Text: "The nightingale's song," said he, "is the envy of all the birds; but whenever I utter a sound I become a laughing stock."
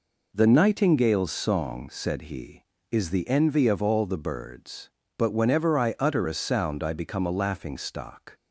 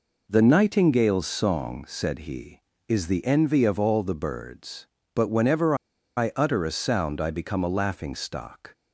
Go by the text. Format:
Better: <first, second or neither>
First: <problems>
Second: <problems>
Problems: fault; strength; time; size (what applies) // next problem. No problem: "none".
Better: first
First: none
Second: pauses between "whenever" and "I"; at 5.7 s; 0.42 s long